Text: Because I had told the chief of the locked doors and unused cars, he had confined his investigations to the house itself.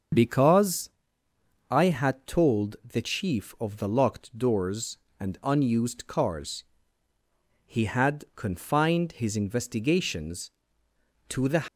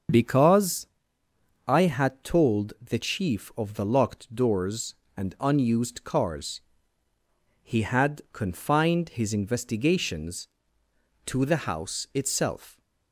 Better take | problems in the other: second | starts louder than the rest; until 1.9 s; 7 dB; also in the second // pauses between "Because" and "I"; noticeable; at 0.8 s; 0.82 s long; noticeable in the second // stops before "house itself"; at 11.6 s

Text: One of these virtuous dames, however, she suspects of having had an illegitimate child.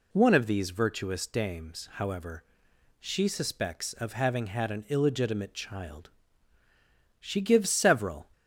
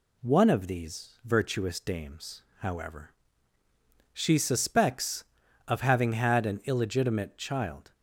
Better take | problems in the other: second | goes on to say "She gives several"; noticeable; from 7.2 s on; 1.0 s long

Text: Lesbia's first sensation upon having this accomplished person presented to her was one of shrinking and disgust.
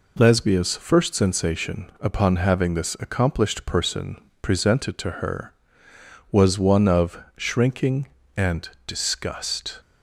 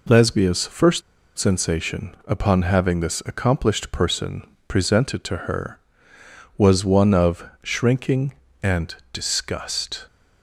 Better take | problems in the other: first | pauses between "first" and "sensation"; slight; at 1.0 s; 0.35 s long // pauses between "person" and "presented"; slight; at 4.4 s; 0.20 s long; slight in the first // pauses between "of" and "shrinking"; slight; at 7.4 s; 0.16 s long; slight in the first // pauses between "and" and "disgust"; slight; at 8.9 s; 0.18 s long; slight in the first

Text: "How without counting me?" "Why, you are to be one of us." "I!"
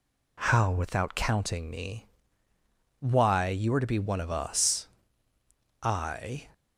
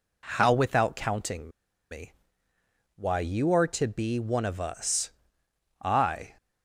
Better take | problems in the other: first | pauses between "counting" and "me"; at 1.4 s; 0.40 s long

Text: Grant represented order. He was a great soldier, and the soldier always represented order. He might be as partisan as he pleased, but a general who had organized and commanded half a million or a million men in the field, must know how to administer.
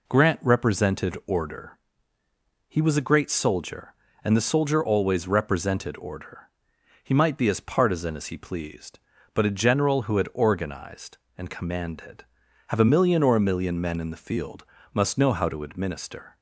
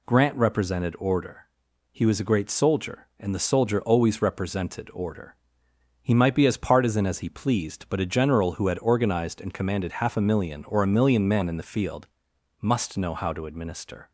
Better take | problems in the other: second | says "have" for "half"; at 12.6 s

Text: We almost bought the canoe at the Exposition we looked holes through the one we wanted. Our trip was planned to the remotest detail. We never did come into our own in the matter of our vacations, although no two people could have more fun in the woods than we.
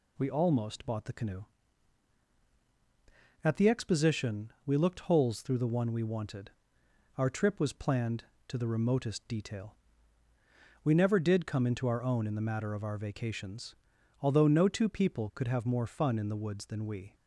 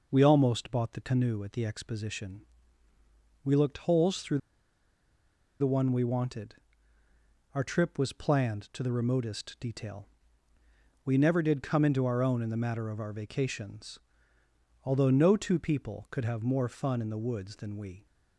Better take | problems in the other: first | pauses between "Exposition" and "we"; at 2.4 s; 1.0 s long // pauses between "through" and "the"; at 4.3 s; 1.2 s long

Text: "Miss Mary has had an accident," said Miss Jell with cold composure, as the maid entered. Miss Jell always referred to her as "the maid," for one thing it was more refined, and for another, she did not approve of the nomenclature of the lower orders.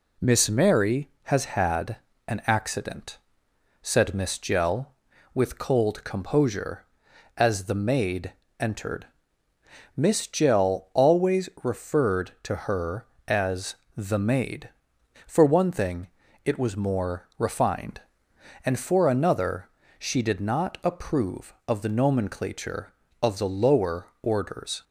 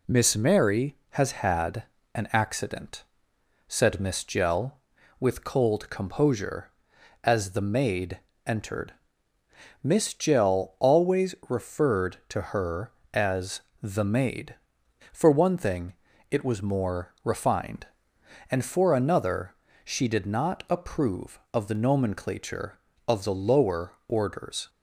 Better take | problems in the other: neither | pauses between "had" and "an"; slight; the same in both // pauses between "maid" and "entered"; slight; the same in both // pauses between "as" and "the"; slight; the same in both // pauses between "thing" and "it"; the same in both

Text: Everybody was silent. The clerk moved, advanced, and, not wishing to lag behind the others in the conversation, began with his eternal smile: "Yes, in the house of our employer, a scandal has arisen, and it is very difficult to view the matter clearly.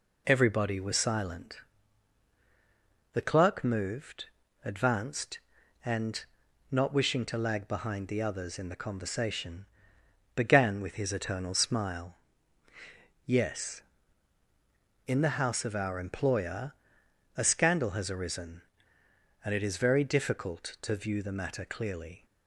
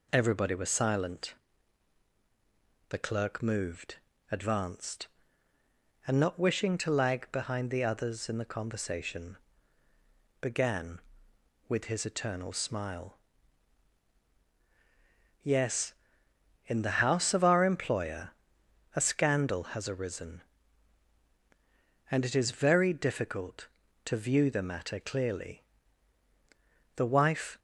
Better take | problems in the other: first | goes on to say "The wife"; noticeable; from 26.9 s on; 0.64 s long

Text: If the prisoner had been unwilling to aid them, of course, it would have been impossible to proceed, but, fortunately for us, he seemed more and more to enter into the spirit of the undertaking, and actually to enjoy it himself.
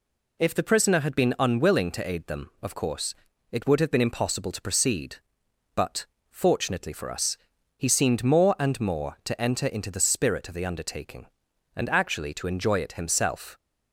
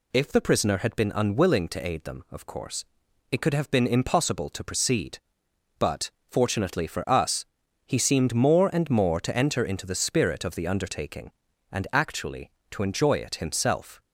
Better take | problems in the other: first | says "could" for "would"; at 3.4 s

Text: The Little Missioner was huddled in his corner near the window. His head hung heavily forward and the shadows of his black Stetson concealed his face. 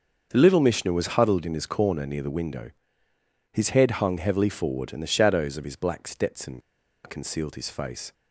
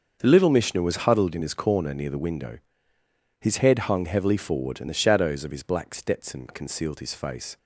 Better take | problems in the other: second | starts louder than the rest; until 1.3 s; 6.5 dB; also in the second // pauses between "Stetson" and "concealed"; at 6.6 s; 0.43 s long

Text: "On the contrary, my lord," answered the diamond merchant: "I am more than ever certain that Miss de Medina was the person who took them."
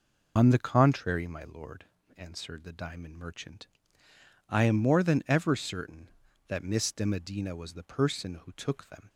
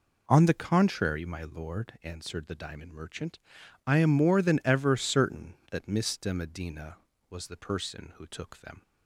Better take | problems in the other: second | loses the start of "On"; at 0.3 s; 85 ms

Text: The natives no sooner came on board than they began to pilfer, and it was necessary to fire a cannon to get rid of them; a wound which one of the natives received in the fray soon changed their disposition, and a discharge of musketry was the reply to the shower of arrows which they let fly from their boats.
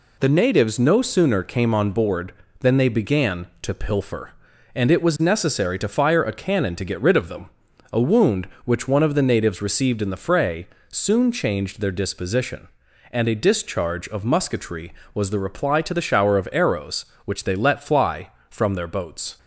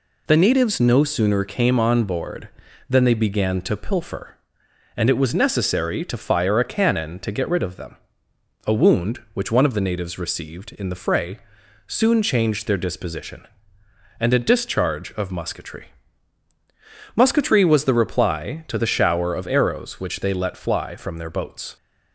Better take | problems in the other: first | pauses between "fray" and "soon"; noticeable; at 11.3 s; 0.50 s long; slight in the first // says "musketry" twice; at 17.1 s

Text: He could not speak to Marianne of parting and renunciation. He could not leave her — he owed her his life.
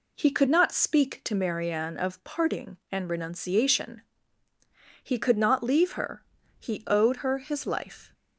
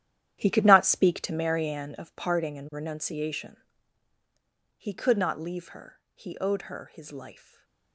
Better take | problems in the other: first | gets quieter; strong; throughout; 13.5 dB // stays silent after the last word; slight; from 7.3 s on; 0.6 s long

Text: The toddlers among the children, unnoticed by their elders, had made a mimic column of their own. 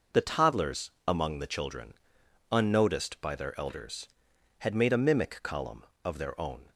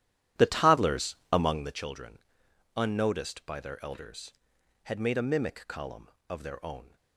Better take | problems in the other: first | starts louder than the rest; strong; until 1.8 s; 12 dB // pauses between "toddlers" and "among"; slight; at 1.1 s; 0.16 s long; slight in the first

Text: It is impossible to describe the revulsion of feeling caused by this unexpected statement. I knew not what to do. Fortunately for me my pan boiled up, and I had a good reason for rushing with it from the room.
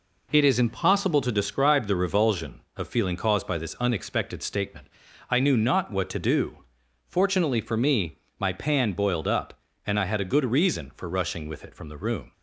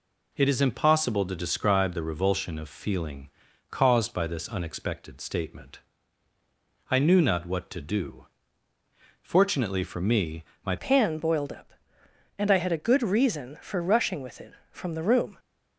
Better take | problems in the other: first | pauses between "feeling" and "caused"; at 3.2 s; 0.42 s long // pauses between "me" and "my"; slight; at 10.4 s; 0.20 s long; slight in the first // changes voice at "pan"; from 10.7 s on; 4.6 s long

